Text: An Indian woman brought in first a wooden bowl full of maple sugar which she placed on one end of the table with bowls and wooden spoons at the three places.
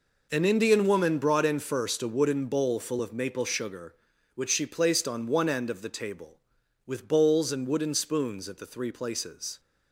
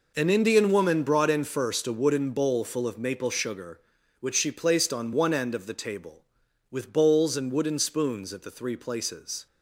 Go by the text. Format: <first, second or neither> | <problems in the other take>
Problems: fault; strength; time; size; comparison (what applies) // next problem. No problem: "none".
neither | none